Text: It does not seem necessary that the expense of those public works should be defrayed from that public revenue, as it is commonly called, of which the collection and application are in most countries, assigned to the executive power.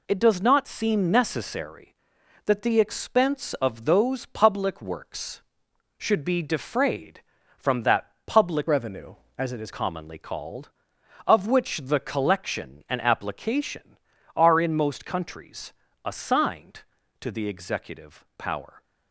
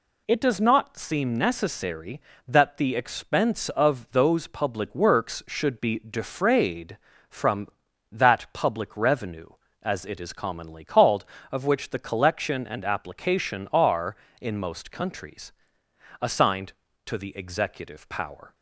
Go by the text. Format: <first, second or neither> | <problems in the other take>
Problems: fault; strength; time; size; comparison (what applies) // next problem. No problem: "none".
second | changes voice from "revenue" to "is"; from 8.6 to 9.7 s; 1.1 s long